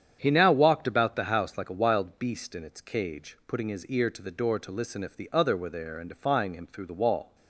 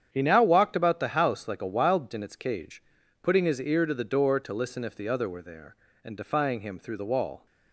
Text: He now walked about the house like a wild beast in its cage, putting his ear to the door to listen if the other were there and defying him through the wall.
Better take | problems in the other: first | starts louder than the rest; strong; until 1.1 s; 8.5 dB; strong in the first // skips "beast"; at 2.1 s

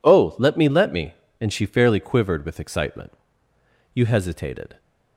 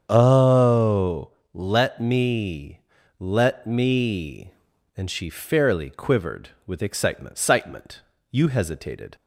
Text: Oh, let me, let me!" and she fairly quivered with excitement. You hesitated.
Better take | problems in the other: first | starts louder than the rest; strong; until 1.0 s; 7.5 dB // says "excitement" twice; at 7.3 s

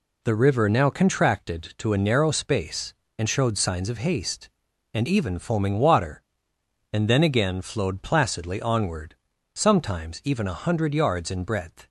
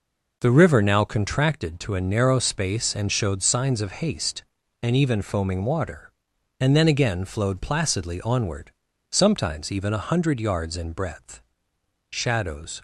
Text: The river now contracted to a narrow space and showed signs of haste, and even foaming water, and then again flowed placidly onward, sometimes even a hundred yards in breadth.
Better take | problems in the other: first | goes on to say "Shadows"; noticeable; from 12.0 s on; 0.72 s long

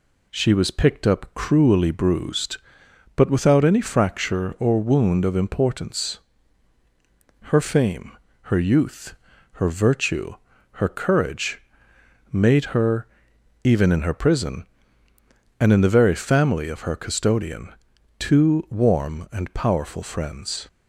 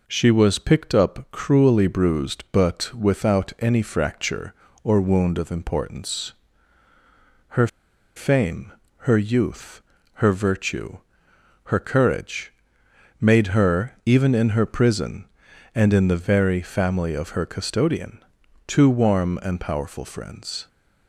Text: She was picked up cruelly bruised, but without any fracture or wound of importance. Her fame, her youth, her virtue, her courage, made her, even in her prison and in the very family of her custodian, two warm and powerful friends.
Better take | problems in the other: first | pauses between "Her" and "fame"; noticeable; at 7.6 s; 0.49 s long

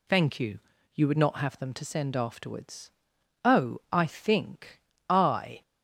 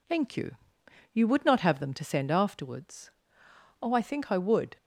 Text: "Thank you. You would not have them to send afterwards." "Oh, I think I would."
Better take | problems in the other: second | pauses between "think" and "I"; slight; at 4.7 s; 0.28 s long // stops before "would"; at 5.6 s

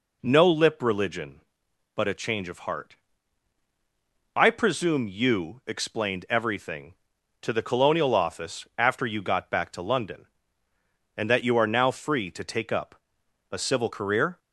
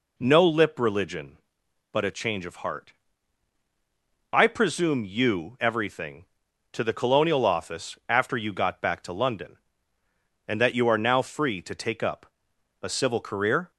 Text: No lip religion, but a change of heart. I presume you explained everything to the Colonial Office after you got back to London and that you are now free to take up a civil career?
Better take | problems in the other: first | skips "explained"; at 5.5 s // pauses between "up" and "a"; noticeable; at 12.2 s; 0.56 s long; noticeable in the first

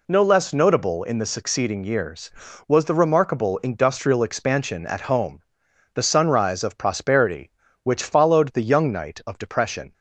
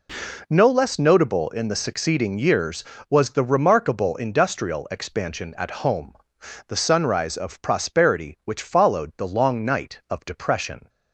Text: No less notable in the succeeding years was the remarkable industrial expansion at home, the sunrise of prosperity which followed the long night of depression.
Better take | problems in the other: second | says "young" for "long"; at 8.6 s

